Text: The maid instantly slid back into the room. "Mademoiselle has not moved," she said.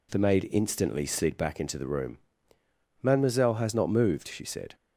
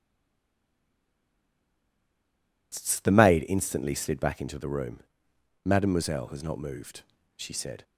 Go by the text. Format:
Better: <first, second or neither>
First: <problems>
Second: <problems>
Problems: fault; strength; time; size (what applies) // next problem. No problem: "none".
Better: first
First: none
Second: stays silent before the first word; strong; until 2.7 s; 2.7 s long